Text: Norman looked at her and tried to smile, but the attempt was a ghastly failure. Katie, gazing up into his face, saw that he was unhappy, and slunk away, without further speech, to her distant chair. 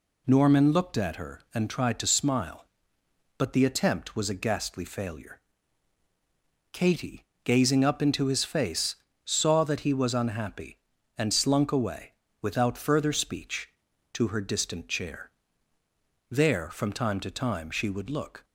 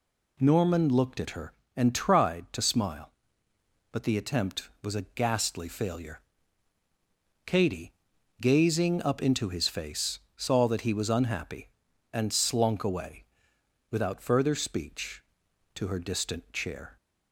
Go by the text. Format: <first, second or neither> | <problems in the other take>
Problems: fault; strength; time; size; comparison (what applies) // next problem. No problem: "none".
second | goes on to say "There from time to time she would look"; strong; from 16.3 s on; 2.1 s long